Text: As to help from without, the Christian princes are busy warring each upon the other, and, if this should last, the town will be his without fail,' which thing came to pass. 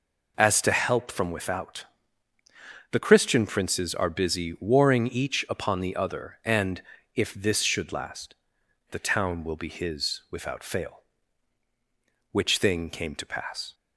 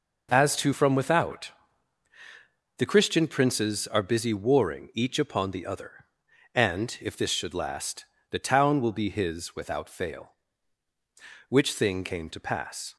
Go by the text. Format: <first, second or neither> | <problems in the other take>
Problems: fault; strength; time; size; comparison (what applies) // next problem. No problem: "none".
first | skips "help"; at 0.7 s